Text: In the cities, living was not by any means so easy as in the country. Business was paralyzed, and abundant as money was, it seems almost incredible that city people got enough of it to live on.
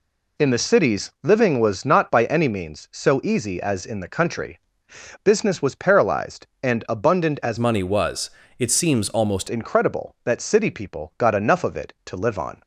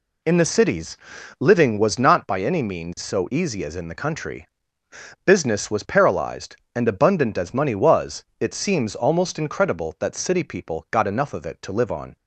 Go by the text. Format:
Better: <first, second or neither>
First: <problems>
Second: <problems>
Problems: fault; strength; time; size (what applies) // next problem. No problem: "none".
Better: second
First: changes voice from "money" to "almost"; from 7.5 to 9.4 s; 1.9 s long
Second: none